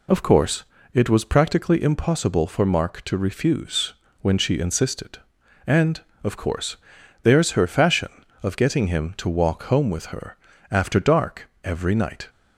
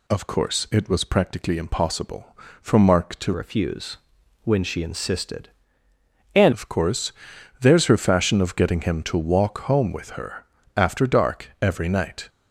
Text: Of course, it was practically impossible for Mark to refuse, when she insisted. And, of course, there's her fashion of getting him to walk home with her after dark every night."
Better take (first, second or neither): first